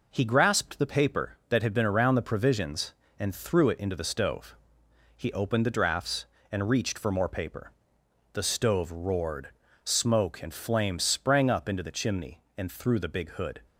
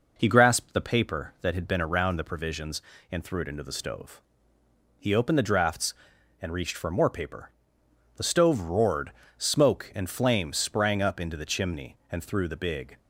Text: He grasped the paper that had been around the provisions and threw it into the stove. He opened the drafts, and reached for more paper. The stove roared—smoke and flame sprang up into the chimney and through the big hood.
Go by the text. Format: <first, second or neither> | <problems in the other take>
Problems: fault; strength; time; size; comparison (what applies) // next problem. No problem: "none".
first | stops before "hood"; at 12.9 s